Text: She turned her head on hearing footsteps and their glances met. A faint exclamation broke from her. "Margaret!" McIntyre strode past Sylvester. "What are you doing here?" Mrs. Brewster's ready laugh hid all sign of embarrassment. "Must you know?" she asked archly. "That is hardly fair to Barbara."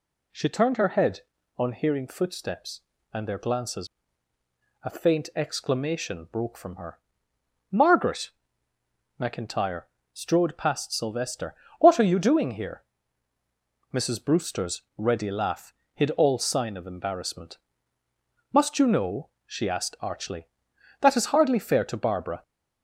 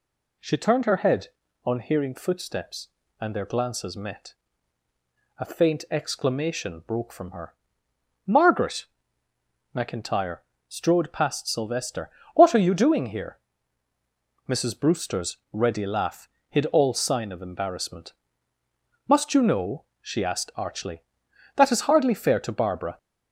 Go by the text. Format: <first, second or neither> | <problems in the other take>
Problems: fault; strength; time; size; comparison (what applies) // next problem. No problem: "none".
second | skips "met"; at 4.3 s // pauses between "McIntyre" and "strode"; slight; at 9.8 s; 0.30 s long; slight in the second // pauses between "laugh" and "hid"; slight; at 15.7 s; 0.20 s long; slight in the second